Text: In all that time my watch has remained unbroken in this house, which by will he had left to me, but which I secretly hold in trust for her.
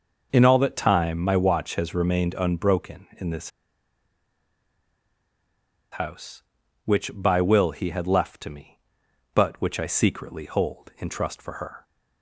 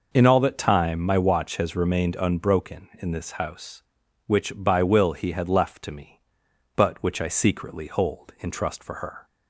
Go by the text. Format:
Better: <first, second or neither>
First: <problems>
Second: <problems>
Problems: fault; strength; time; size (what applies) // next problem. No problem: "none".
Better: second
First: pauses between "this" and "house"; strong; at 3.4 s; 2.4 s long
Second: none